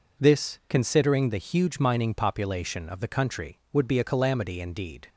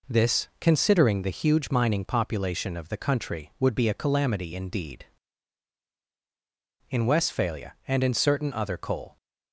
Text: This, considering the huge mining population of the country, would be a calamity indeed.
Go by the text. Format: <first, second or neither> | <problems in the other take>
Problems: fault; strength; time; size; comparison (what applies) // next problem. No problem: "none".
first | goes on to say "In Westphalia and in certain other coal"; strong; from 6.8 s on; 2.2 s long